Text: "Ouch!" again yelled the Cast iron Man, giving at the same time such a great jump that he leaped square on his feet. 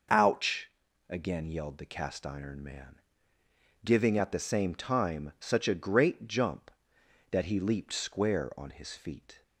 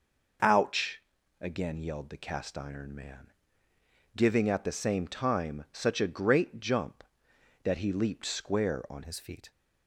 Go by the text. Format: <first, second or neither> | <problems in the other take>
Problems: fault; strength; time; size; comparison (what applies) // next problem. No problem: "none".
first | changes voice at "his"; from 9.0 s on; 0.5 s long